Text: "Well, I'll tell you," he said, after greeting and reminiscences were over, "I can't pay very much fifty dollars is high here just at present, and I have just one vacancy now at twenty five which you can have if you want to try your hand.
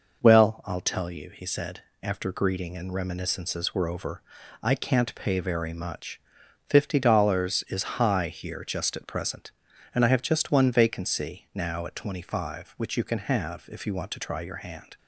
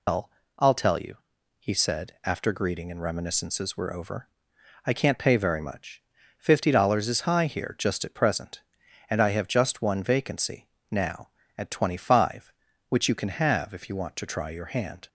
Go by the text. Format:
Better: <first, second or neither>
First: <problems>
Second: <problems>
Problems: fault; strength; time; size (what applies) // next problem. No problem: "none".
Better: first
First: pauses between "much" and "fifty"; noticeable; at 6.1 s; 0.48 s long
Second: loses the start of "Well"; at 0.0 s; 155 ms // pauses between "much" and "fifty"; at 5.9 s; 0.38 s long // pauses between "vacancy" and "now"; slight; at 10.6 s; 0.24 s long